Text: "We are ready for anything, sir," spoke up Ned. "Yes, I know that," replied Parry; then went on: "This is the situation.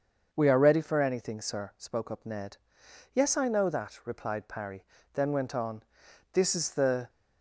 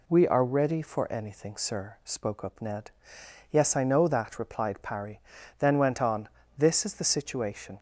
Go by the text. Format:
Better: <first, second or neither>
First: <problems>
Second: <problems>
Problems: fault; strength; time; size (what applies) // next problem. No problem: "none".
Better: second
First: starts louder than the rest; until 1.3 s; 6.5 dB // stops before "situation"; at 7.0 s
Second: none